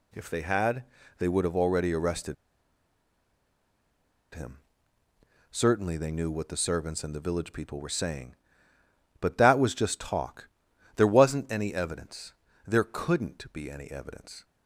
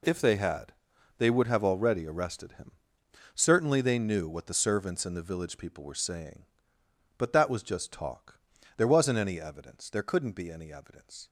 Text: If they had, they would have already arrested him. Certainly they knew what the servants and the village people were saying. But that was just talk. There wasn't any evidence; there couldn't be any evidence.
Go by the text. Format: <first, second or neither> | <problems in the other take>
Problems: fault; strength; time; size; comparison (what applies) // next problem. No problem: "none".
second | pauses between "arrested" and "him"; strong; at 2.3 s; 1.9 s long